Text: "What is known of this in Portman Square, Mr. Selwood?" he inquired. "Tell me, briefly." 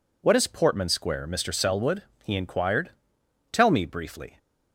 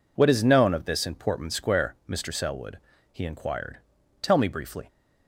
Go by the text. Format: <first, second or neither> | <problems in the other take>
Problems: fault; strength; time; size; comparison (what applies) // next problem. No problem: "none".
second | skips "known of this in"; at 0.4 s